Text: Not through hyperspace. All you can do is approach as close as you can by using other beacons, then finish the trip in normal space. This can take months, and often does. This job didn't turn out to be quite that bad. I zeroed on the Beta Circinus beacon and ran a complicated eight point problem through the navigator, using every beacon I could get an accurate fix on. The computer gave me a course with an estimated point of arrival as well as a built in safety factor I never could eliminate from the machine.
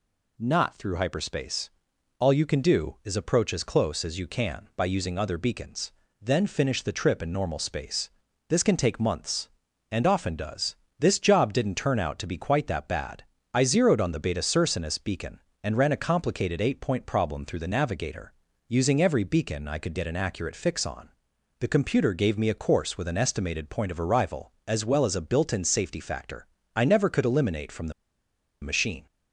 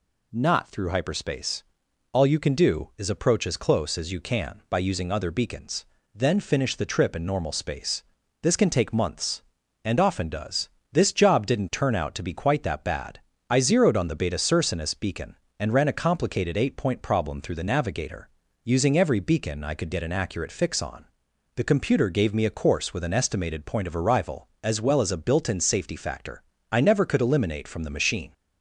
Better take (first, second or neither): second